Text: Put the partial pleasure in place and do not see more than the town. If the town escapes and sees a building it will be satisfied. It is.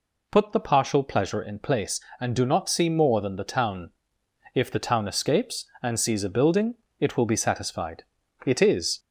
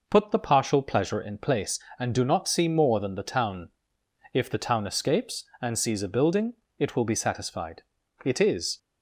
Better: second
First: gets louder; slight; throughout; 2.5 dB // pauses between "building" and "it"; slight; at 6.7 s; 0.24 s long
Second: pauses between "building" and "it"; slight; at 6.5 s; 0.24 s long

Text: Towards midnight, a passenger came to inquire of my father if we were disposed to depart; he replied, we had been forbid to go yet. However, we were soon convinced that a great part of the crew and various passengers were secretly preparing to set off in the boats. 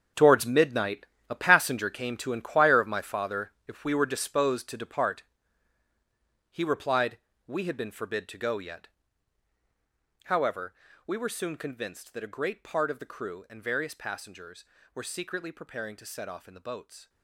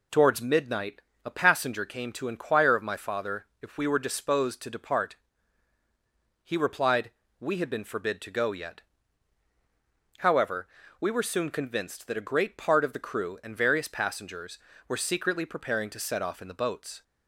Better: second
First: gets quieter; strong; throughout; 13 dB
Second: none

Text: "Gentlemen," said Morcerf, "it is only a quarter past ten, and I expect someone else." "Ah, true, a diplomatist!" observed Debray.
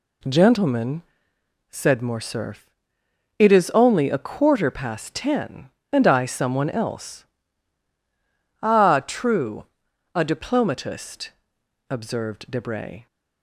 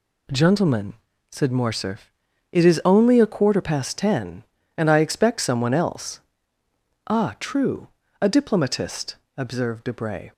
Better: second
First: skips "expect"; at 6.2 s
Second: none

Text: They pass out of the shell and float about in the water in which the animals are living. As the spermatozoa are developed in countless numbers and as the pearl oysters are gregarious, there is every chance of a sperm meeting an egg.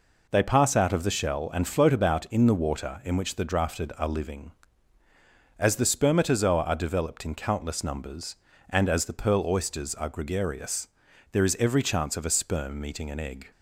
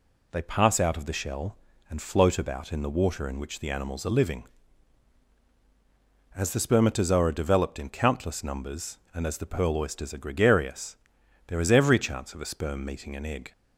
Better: second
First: says "drafted" for "animals"; at 3.4 s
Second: none

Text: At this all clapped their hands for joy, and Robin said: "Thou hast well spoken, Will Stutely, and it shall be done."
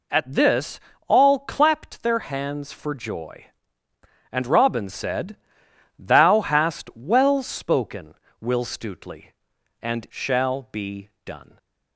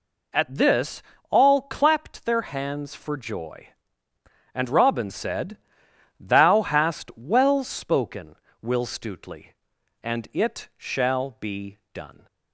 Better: second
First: pauses between "this" and "all"; slight; at 0.7 s; 0.28 s long // skips "it"; at 10.0 s // pauses between "be" and "done"; slight; at 11.0 s; 0.16 s long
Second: pauses between "this" and "all"; slight; at 1.0 s; 0.28 s long // pauses between "be" and "done"; slight; at 11.7 s; 0.16 s long

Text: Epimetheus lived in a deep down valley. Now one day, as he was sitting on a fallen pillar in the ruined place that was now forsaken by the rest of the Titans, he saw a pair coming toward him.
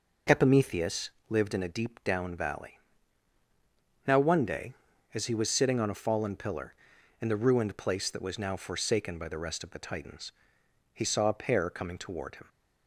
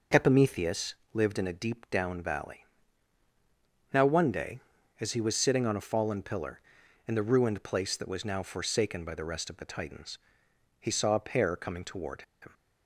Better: first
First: pauses between "Epimetheus" and "lived"; slight; at 1.0 s; 0.20 s long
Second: pauses between "Epimetheus" and "lived"; slight; at 0.9 s; 0.20 s long // pauses between "toward" and "him"; slight; at 12.2 s; 0.19 s long

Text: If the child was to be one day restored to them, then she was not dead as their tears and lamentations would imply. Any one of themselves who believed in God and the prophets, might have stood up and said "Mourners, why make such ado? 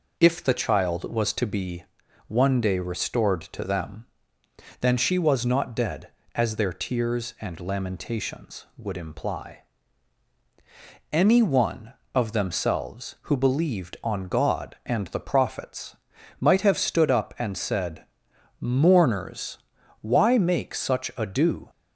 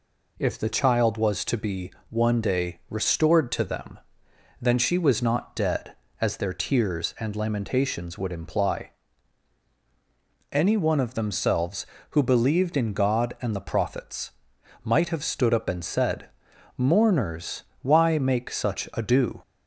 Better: second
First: pauses between "be" and "one"; at 1.8 s; 0.42 s long // says "on" for "in"; at 14.0 s // pauses between "said" and "Mourners"; noticeable; at 18.0 s; 0.56 s long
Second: pauses between "be" and "one"; slight; at 1.9 s; 0.20 s long // pauses between "said" and "Mourners"; noticeable; at 16.2 s; 0.48 s long

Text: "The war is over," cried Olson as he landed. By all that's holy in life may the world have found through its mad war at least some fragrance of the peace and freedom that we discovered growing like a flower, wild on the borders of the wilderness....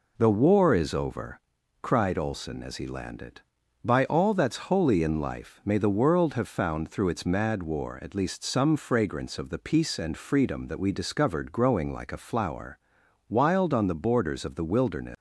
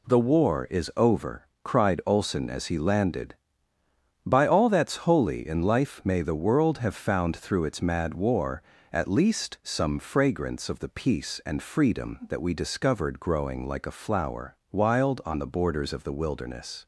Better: neither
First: none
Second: none

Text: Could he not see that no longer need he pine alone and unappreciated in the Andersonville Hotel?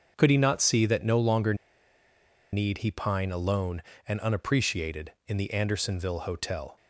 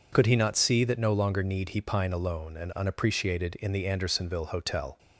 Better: second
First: starts louder than the rest; until 1.1 s; 6.5 dB // pauses between "longer" and "need"; at 1.5 s; 0.98 s long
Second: none

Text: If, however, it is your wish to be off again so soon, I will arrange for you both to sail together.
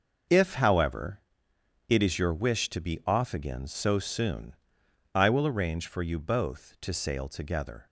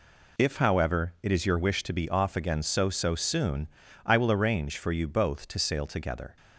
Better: first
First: none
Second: says "so" twice; at 2.8 s

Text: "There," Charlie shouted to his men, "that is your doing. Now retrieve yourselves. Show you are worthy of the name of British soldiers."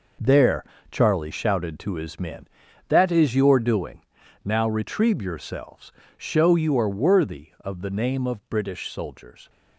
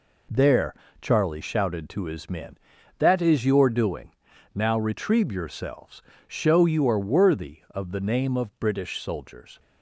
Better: second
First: gets quieter; strong; throughout; 10.5 dB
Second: none

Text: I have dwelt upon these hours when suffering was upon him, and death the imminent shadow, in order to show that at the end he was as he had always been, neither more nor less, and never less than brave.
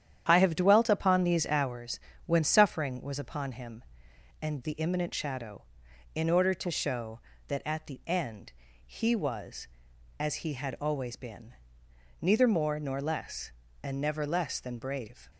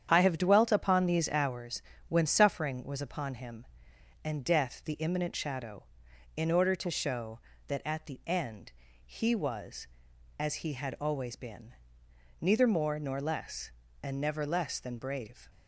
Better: second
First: starts louder than the rest; strong; until 1.2 s; 9.5 dB // pauses between "hours" and "when"; slight; at 2.0 s; 0.24 s long // skips "death"; at 4.6 s // pauses between "end" and "he"; slight; at 8.5 s; 0.32 s long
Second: starts louder than the rest; strong; until 1.1 s; 8.5 dB // pauses between "hours" and "when"; slight; at 1.8 s; 0.24 s long // pauses between "end" and "he"; slight; at 8.7 s; 0.32 s long

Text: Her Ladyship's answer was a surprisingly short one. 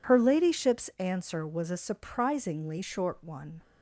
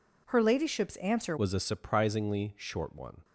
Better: first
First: none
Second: changes voice at "was"; from 1.3 s on; 1.9 s long

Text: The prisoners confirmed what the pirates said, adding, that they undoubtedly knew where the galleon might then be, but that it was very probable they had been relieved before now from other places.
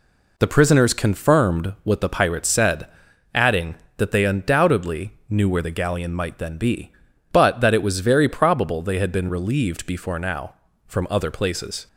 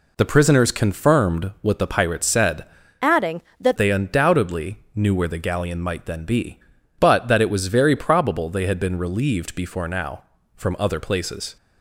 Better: first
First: pauses between "undoubtedly" and "knew"; slight; at 5.1 s; 0.18 s long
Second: changes voice from "adding" to "that"; from 3.0 to 3.7 s; 0.7 s long // pauses between "undoubtedly" and "knew"; slight; at 4.7 s; 0.18 s long

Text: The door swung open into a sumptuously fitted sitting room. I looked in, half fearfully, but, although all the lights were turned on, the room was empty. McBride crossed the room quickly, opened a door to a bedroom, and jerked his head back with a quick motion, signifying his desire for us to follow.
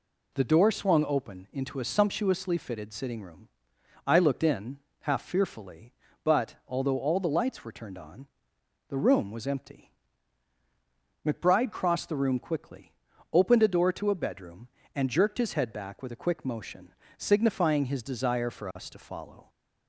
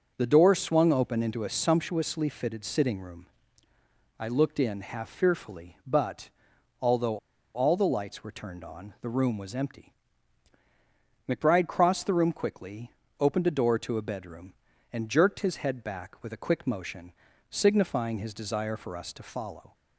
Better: first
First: none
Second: pauses between "although" and "all"; at 7.1 s; 0.36 s long

